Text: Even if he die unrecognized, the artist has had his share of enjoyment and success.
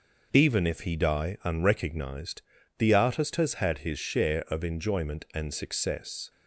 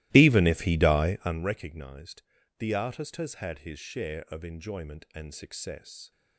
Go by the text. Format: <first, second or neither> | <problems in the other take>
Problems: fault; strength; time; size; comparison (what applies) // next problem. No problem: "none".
first | starts louder than the rest; strong; until 1.5 s; 17.5 dB